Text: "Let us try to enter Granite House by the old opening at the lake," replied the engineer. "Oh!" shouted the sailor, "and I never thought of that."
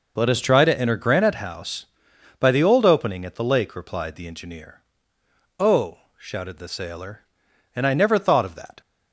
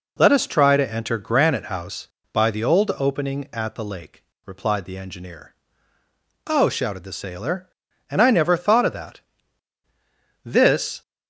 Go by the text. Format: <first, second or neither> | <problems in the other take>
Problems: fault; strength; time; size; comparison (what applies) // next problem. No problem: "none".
first | goes on to say "This"; from 10.4 s on; 0.58 s long